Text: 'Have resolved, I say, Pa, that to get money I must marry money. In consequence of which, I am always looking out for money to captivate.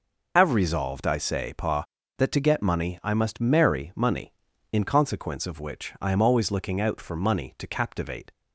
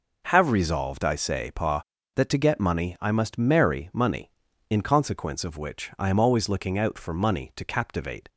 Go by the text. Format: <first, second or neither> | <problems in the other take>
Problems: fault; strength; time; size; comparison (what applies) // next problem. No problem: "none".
second | loses the start of "Have"; at 0.3 s; 90 ms